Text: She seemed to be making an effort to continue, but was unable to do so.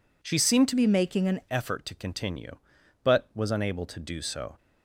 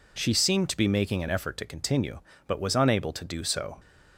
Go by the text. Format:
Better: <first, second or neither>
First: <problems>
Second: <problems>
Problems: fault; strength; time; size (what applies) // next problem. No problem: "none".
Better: second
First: changes voice from "be" to "an"; from 0.7 to 1.4 s; 0.7 s long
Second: none